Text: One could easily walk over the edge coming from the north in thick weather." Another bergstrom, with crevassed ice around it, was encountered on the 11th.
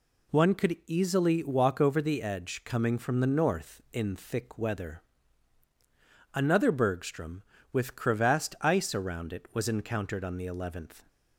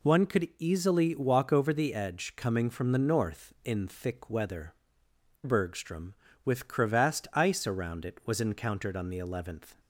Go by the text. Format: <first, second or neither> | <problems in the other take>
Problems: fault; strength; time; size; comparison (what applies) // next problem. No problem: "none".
first | skips "Another"; at 5.0 s